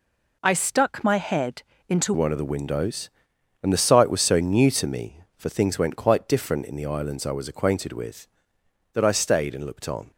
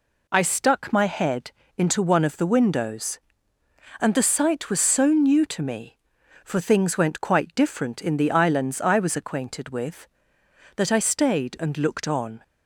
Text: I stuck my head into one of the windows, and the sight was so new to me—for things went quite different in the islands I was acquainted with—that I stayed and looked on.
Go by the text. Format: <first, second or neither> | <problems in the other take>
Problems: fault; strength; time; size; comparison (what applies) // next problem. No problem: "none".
second | pauses between "head" and "into"; slight; at 1.6 s; 0.26 s long; slight in the second // changes voice at "one"; from 2.1 s on; 8.0 s long